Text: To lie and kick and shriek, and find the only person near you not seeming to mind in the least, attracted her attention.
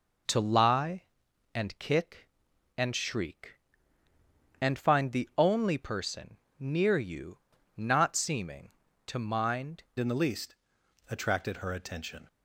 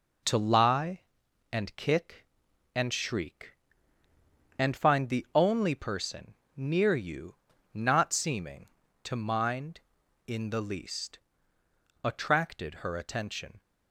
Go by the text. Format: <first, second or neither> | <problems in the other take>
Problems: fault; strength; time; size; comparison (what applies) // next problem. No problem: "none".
second | pauses between "person" and "near"; slight; at 6.3 s; 0.22 s long; slight in the second // pauses between "you" and "not"; at 7.3 s; 0.40 s long; also in the second // changes voice at "in"; from 9.9 s on; 2.3 s long